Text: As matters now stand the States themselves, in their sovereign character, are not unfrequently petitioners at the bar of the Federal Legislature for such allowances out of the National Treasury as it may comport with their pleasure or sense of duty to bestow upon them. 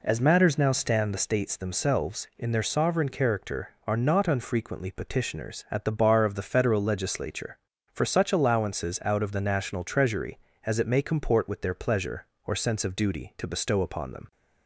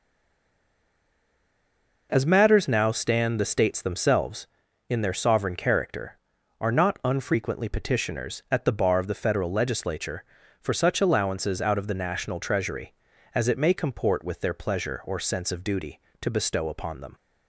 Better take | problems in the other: first | stays silent before the first word; noticeable; until 2.0 s; 2.0 s long

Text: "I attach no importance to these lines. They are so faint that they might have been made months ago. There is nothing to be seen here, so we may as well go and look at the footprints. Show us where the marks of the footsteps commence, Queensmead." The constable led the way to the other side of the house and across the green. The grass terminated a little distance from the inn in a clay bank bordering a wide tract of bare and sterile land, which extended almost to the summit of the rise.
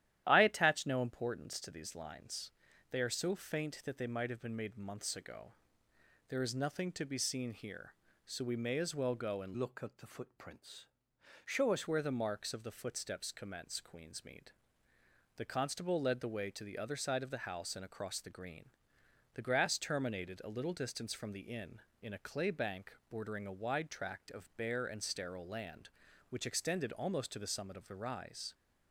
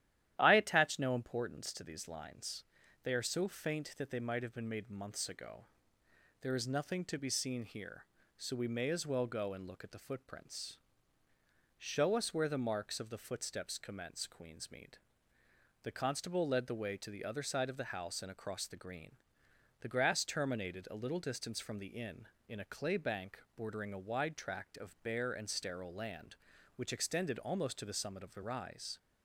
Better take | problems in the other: second | starts louder than the rest; strong; until 1.2 s; 12 dB; strong in the second // changes voice from "look" to "us"; from 9.5 to 11.8 s; 2.3 s long // pauses between "bank" and "bordering"; slight; at 22.9 s; 0.16 s long; slight in the second

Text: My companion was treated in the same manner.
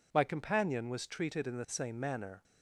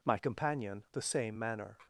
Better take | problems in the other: first | skips "was treated in"; at 0.8 s

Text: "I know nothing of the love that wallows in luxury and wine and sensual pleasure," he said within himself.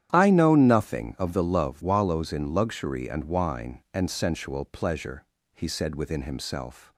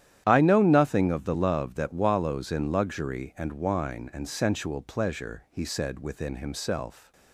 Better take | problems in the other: second | starts louder than the rest; strong; until 1.1 s; 11 dB; strong in the second // skips "that"; at 1.8 s

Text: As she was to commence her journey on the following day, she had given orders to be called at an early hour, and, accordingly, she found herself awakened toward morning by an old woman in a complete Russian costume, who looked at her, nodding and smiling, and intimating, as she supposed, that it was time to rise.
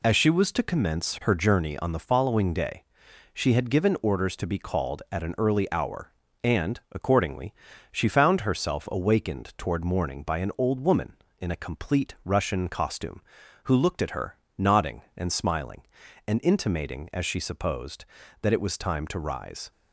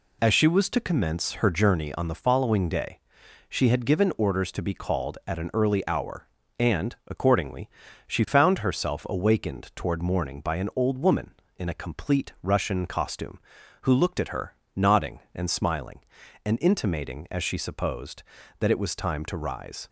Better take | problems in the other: neither | none

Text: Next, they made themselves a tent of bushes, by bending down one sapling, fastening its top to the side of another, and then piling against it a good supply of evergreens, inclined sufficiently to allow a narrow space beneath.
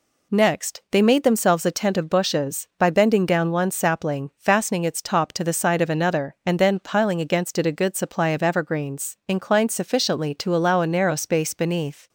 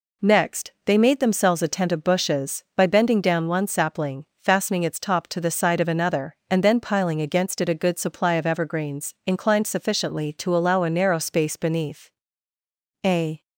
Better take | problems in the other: first | goes on to say "A"; slight; from 13.0 s on; 0.38 s long

